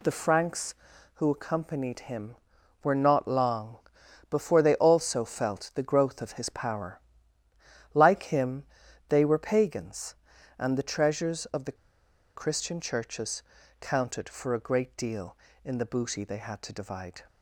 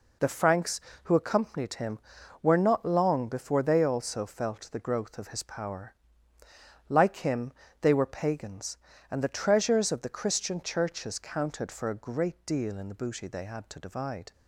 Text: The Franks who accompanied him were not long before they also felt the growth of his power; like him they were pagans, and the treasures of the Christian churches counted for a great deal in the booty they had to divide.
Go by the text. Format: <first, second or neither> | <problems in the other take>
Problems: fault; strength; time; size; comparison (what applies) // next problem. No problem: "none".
second | pauses between "long" and "before"; noticeable; at 3.7 s; 0.52 s long // pauses between "him" and "they"; noticeable; at 8.6 s; 0.46 s long; slight in the second // pauses between "the" and "Christian"; noticeable; at 11.7 s; 0.61 s long // pauses between "churches" and "counted"; at 13.4 s; 0.38 s long